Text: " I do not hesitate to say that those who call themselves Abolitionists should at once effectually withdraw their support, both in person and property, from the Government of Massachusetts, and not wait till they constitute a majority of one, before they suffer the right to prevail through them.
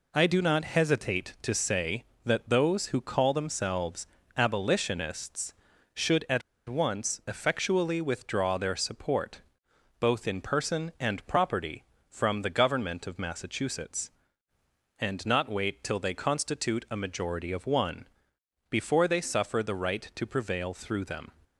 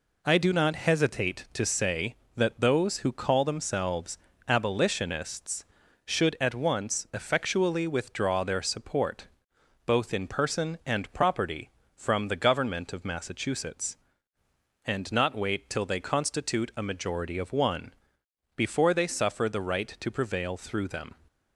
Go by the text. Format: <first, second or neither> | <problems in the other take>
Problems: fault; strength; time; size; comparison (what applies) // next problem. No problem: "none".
second | pauses between "themselves" and "Abolitionists"; slight; at 4.0 s; 0.28 s long; slight in the second // pauses between "at" and "once"; slight; at 6.4 s; 0.26 s long